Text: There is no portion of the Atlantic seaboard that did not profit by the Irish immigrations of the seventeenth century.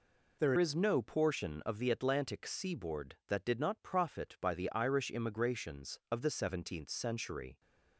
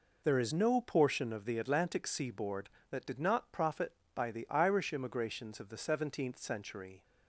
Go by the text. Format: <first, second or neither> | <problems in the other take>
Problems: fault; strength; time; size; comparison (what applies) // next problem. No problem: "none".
second | changes voice at "is"; from 0.5 s on; 7.0 s long